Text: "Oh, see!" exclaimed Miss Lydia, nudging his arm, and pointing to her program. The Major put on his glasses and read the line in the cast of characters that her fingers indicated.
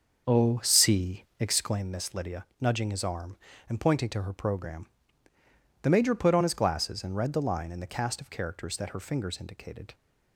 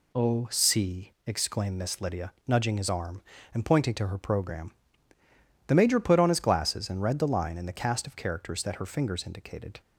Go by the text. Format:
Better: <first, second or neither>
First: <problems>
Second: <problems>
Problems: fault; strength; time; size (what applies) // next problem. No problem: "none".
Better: second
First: starts louder than the rest; until 1.8 s; 6.5 dB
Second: none